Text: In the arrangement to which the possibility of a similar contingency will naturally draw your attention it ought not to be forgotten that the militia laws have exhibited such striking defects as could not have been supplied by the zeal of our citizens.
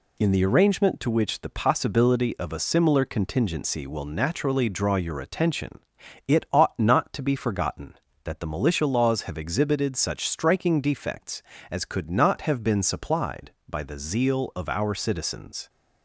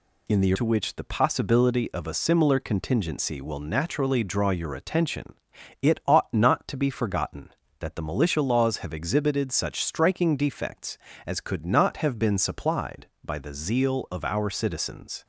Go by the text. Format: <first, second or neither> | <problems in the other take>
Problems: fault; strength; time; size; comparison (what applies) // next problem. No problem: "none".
first | skips "arrangement"; at 0.5 s // pauses between "attention" and "it"; noticeable; at 5.3 s; 0.48 s long; noticeable in the first